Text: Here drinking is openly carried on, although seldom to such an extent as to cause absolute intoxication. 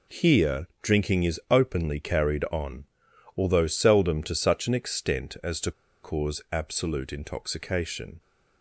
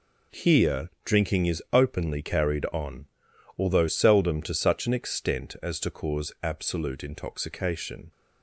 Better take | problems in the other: second | pauses between "to" and "cause"; slight; at 5.7 s; 0.30 s long

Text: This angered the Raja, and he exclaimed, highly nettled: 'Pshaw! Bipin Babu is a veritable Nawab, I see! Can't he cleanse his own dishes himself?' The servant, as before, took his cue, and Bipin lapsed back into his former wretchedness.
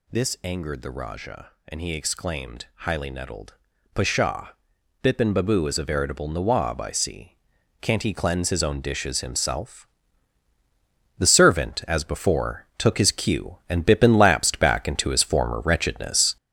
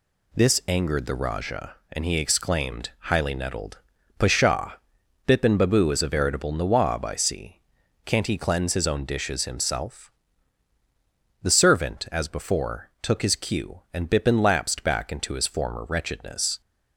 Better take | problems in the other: second | gets louder; throughout; 6.5 dB

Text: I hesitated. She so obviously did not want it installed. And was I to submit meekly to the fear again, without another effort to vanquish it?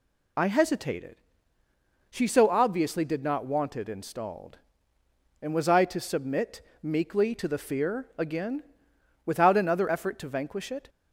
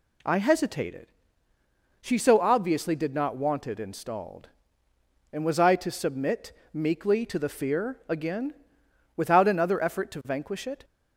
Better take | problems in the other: second | loses the start of "I"; at 0.3 s; 75 ms // pauses between "submit" and "meekly"; slight; at 6.6 s; 0.22 s long; slight in the second

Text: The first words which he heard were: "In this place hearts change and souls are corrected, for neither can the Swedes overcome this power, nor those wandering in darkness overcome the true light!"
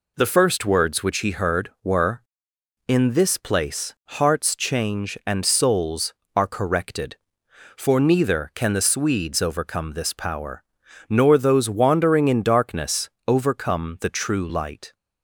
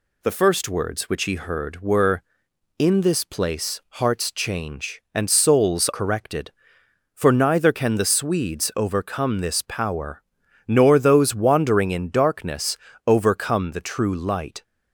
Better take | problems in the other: first | pauses between "place" and "hearts"; slight; at 3.7 s; 0.22 s long; slight in the first // skips "are"; at 5.8 s // pauses between "darkness" and "overcome"; slight; at 12.7 s; 0.30 s long; slight in the first

